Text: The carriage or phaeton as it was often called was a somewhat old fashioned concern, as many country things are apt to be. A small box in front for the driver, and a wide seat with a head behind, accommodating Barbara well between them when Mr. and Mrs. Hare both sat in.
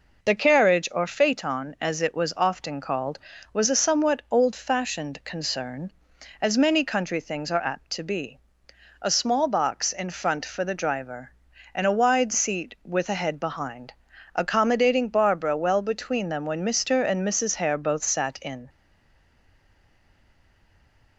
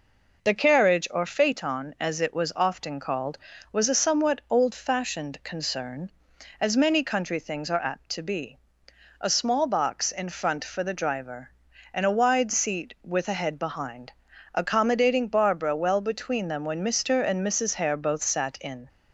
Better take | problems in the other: second | stays silent after the last word; from 18.6 s on; 2.5 s long

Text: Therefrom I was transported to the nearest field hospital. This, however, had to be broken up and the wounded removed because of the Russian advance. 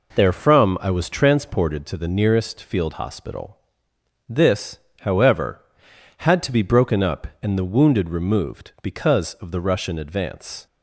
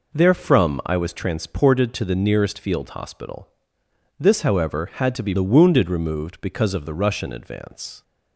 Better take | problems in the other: first | skips "broken up and"; at 5.3 s

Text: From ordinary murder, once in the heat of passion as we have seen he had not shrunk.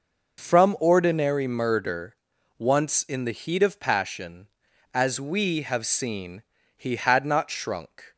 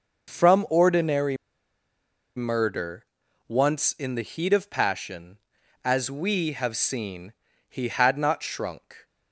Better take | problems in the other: first | pauses between "ordinary" and "murder"; at 1.3 s; 1.0 s long // pauses between "seen" and "he"; slight; at 7.3 s; 0.36 s long; slight in the first

